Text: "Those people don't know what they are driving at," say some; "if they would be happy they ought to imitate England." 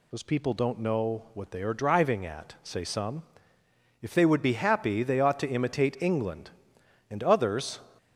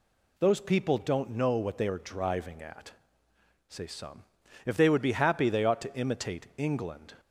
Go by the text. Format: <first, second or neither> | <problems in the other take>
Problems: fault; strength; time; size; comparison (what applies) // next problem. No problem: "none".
second | goes on to say "And others"; noticeable; from 7.0 s on; 0.70 s long